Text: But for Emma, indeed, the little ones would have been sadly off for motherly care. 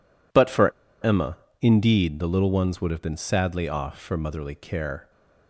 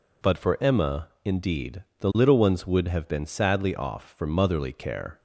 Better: second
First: pauses between "for" and "Emma"; slight; at 0.7 s; 0.33 s long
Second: none

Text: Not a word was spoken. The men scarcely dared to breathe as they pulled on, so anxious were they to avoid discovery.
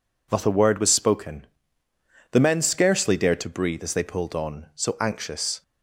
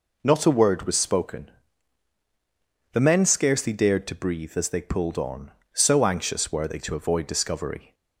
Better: second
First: stops before "were they to avoid discovery"; at 5.6 s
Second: none

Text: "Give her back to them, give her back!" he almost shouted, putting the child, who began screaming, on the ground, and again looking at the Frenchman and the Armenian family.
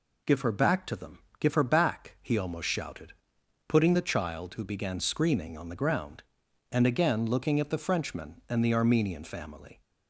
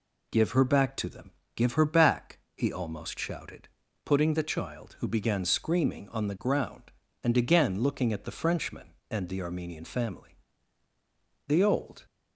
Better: first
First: none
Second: goes on to say "The old"; from 11.4 s on; 0.58 s long

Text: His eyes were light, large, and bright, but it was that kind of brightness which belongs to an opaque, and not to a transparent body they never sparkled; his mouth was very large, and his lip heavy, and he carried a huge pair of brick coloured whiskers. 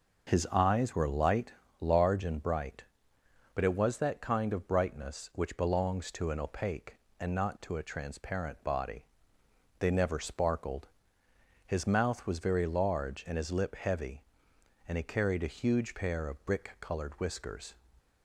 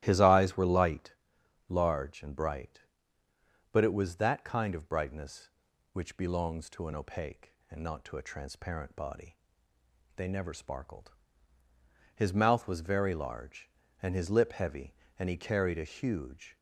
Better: first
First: starts louder than the rest; until 1.3 s; 6 dB // pauses between "body" and "they"; noticeable; at 9.0 s; 0.78 s long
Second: starts louder than the rest; strong; until 1.0 s; 14 dB // pauses between "body" and "they"; noticeable; at 9.3 s; 0.80 s long // stops before "pair of brick coloured whiskers"; at 16.5 s

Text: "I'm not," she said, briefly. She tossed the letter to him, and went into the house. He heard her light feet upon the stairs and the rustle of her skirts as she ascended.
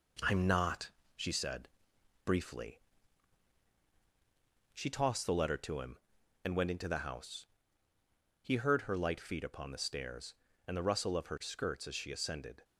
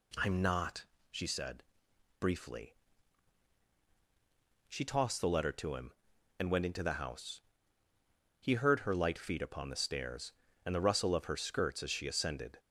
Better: second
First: gets quieter; noticeable; throughout; 4 dB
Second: none

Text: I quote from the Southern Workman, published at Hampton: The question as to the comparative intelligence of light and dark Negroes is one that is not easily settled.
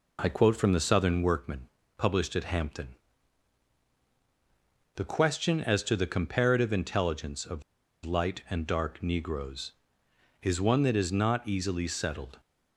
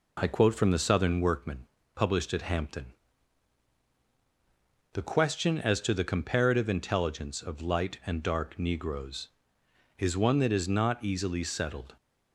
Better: second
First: pauses between "of" and "light"; at 7.6 s; 0.41 s long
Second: none

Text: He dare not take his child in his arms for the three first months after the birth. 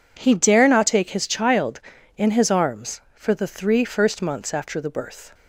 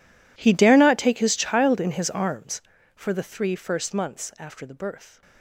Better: first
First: none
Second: gets quieter; strong; throughout; 23 dB

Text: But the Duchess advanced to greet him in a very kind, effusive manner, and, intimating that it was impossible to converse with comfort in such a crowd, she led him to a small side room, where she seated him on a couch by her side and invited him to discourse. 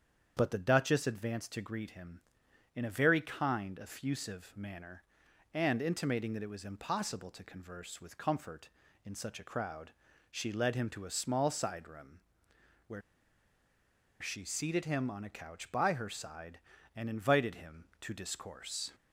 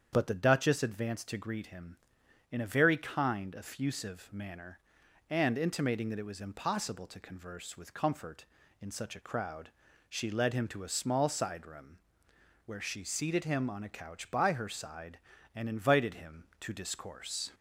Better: second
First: starts louder than the rest; strong; until 1.3 s; 7.5 dB // pauses between "where" and "she"; at 13.0 s; 1.1 s long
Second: starts louder than the rest; strong; until 1.1 s; 7.5 dB

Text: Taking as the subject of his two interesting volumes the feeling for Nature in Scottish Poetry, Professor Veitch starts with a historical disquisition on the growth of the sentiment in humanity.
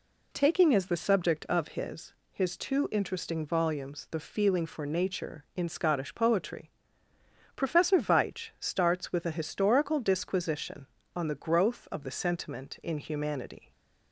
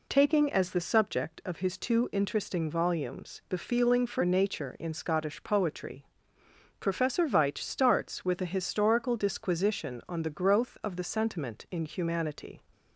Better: second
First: says "his" twice; at 2.3 s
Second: none

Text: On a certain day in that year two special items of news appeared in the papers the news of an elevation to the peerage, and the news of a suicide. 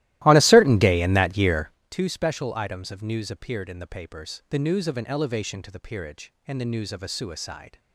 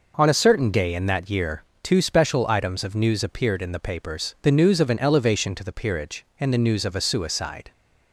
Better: second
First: starts louder than the rest; strong; until 1.8 s; 16 dB // pauses between "year" and "two"; slight; at 1.7 s; 0.20 s long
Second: pauses between "year" and "two"; slight; at 1.6 s; 0.20 s long

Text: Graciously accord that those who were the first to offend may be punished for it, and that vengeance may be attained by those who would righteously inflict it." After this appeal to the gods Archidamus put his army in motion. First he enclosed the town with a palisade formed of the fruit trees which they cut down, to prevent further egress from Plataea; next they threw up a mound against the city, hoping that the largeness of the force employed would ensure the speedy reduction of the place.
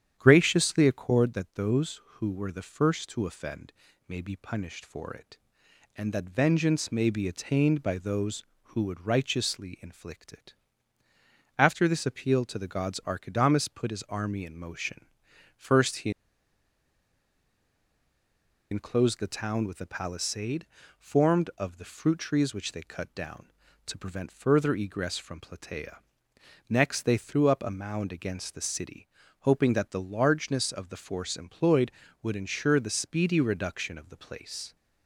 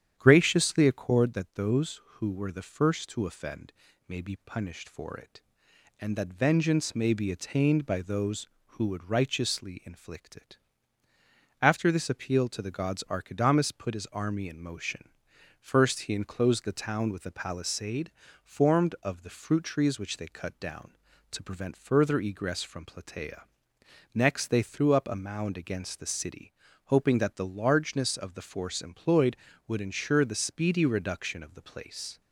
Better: second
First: starts louder than the rest; strong; until 1.1 s; 9.5 dB // pauses between "offend" and "may"; at 3.7 s; 0.38 s long // pauses between "he" and "enclosed"; strong; at 16.1 s; 2.6 s long // pauses between "palisade" and "formed"; slight; at 20.6 s; 0.34 s long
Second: starts louder than the rest; strong; until 1.1 s; 9.5 dB // pauses between "offend" and "may"; at 3.7 s; 0.38 s long // pauses between "palisade" and "formed"; slight; at 18.1 s; 0.34 s long

